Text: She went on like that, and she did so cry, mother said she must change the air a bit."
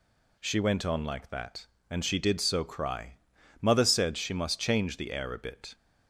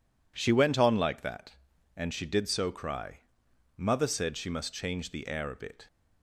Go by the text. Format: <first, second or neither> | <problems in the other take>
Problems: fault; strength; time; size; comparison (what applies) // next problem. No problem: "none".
neither | none